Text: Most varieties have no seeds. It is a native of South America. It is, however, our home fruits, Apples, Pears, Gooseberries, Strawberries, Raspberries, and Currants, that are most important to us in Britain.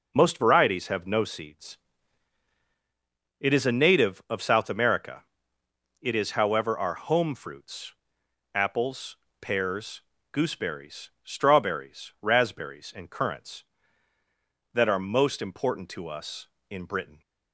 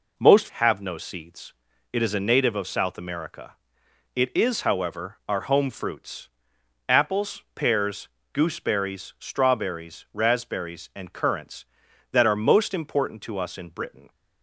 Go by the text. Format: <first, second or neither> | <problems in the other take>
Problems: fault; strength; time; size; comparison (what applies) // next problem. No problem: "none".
first | skips "varieties"; at 0.4 s